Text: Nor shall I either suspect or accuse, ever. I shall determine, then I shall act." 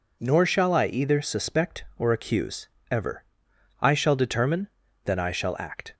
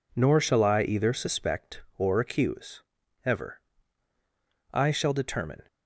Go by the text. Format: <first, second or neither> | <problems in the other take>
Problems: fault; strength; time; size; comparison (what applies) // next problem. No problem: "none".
first | stops before "then I shall act"; at 5.6 s